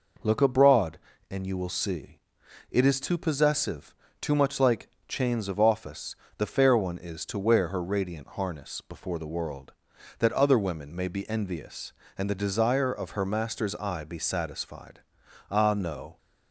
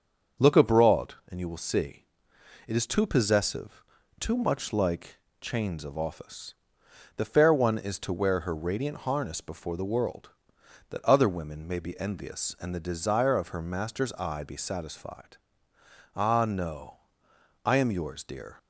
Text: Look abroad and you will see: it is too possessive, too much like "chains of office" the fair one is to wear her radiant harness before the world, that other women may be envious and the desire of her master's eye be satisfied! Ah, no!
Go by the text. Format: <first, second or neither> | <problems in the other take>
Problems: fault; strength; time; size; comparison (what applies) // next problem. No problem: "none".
first | starts louder than the rest; until 1.5 s; 7 dB // pauses between "like" and "chains"; slight; at 5.1 s; 0.24 s long; slight in the first // pauses between "office" and "the"; noticeable; at 6.5 s; 0.62 s long; slight in the first // goes on to say "I am yours dear"; noticeable; from 17.6 s on; 0.94 s long